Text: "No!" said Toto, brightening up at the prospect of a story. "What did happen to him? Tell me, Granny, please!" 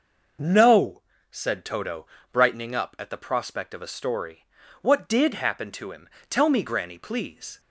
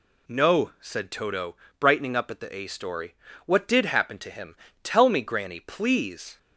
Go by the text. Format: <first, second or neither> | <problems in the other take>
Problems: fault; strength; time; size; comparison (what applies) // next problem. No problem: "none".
first | skips "prospect of"; at 2.5 s